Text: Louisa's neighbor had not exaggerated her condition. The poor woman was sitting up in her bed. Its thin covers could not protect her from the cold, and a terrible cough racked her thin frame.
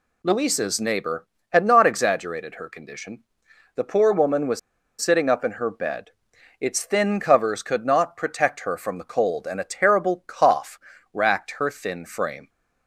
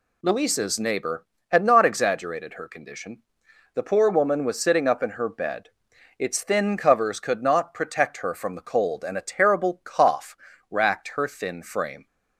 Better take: second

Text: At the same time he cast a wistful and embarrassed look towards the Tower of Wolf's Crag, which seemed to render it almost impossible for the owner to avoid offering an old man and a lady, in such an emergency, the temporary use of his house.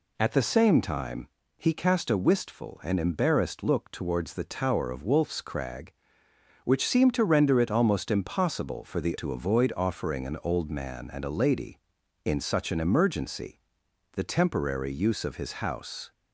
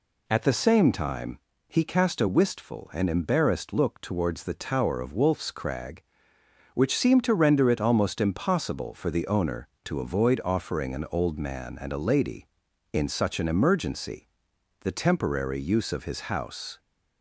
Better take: second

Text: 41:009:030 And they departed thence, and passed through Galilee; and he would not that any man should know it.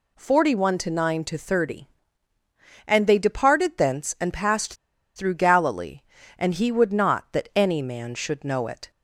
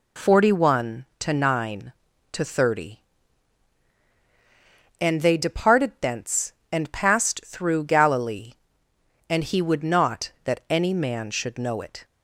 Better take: second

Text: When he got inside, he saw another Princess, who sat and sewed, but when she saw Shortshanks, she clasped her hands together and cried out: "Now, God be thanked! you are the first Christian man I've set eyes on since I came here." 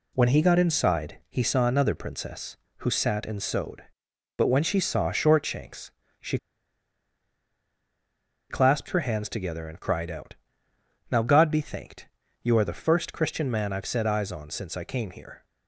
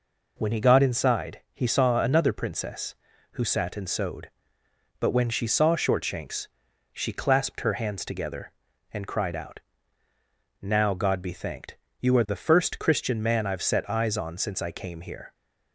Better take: second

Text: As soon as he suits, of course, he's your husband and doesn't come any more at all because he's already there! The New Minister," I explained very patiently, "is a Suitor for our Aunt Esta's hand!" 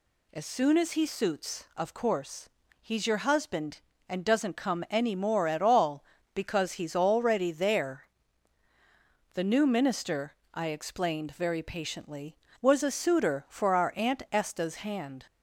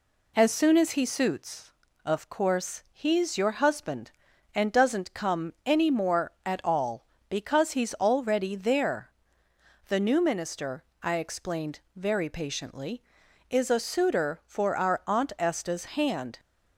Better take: second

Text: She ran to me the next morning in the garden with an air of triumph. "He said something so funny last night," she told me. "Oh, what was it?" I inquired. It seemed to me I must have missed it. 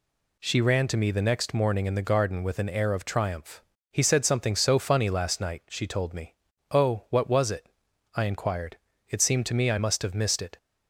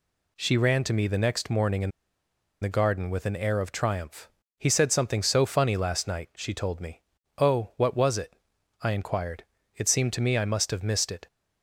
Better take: first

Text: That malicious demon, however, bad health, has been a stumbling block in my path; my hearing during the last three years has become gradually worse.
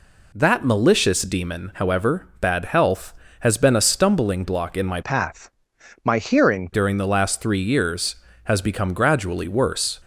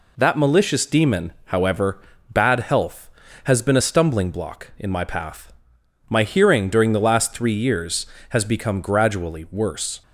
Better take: second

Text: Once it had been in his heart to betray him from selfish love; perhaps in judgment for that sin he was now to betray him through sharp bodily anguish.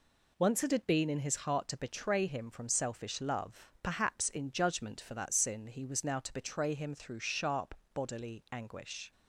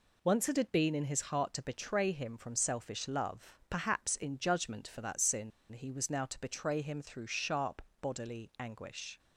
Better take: first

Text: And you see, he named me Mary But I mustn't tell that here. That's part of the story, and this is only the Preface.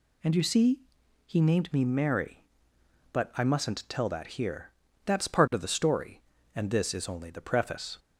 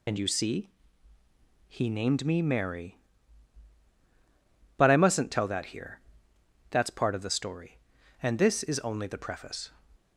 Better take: first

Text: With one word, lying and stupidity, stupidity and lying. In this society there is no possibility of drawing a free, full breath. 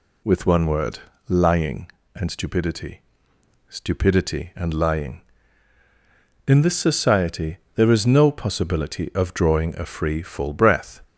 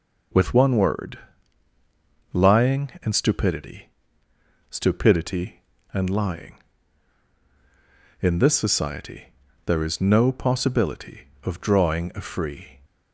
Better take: first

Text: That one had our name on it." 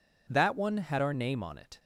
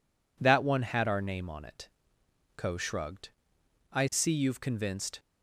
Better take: first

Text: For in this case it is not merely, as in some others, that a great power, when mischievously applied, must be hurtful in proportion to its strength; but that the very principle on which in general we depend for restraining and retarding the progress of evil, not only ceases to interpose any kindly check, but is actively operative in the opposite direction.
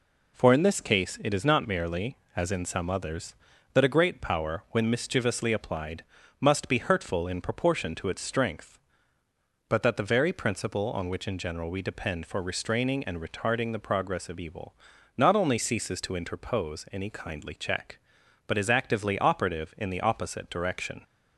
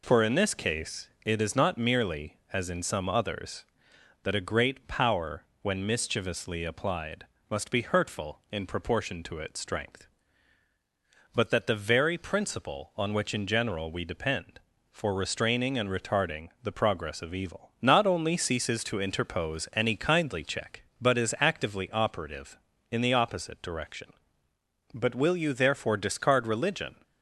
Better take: first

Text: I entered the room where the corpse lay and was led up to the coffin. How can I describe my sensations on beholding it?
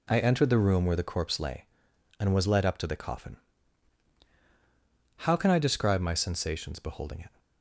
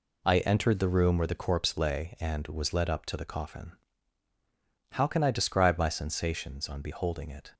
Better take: second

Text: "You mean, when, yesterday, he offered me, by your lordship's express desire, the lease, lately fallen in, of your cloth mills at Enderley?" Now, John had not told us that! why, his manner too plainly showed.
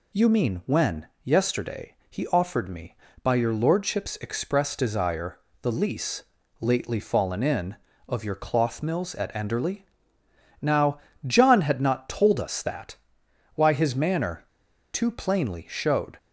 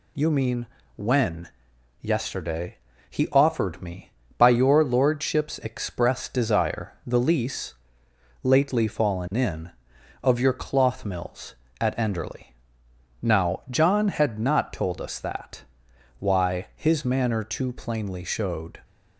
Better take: second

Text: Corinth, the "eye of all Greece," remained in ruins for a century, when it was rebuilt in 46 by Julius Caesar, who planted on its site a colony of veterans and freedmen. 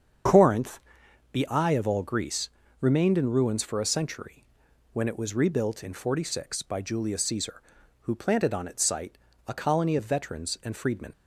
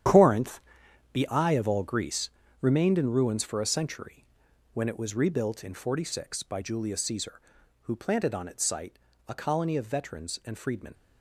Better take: first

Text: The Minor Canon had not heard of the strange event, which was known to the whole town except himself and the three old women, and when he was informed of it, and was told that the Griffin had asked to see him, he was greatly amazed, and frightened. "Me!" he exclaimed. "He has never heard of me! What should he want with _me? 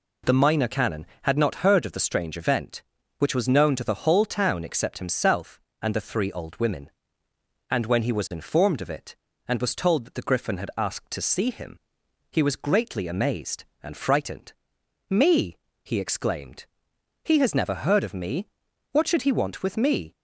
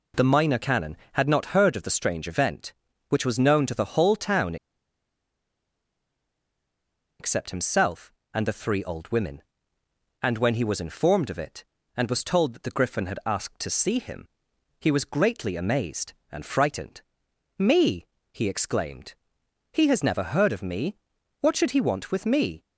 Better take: first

